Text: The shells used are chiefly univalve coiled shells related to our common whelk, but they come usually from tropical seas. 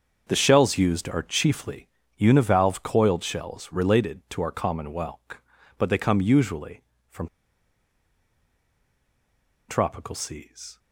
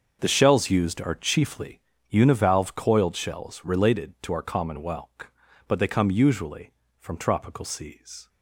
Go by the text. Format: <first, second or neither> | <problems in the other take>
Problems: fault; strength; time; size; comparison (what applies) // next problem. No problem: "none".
second | starts louder than the rest; until 1.2 s; 6.5 dB; also in the second // pauses between "chiefly" and "univalve"; slight; at 1.8 s; 0.30 s long; slight in the second // pauses between "from" and "tropical"; strong; at 7.2 s; 2.3 s long